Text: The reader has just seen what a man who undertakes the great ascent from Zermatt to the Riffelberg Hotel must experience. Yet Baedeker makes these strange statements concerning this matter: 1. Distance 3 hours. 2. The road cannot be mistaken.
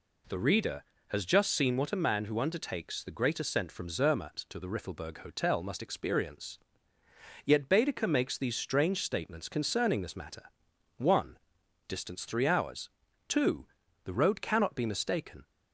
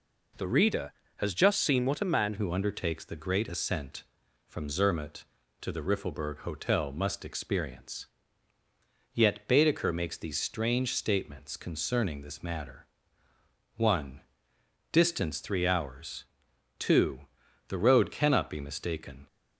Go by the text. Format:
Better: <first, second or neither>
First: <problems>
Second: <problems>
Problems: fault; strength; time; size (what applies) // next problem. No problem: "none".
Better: first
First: none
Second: changes voice at "who"; from 2.3 s on; 16.9 s long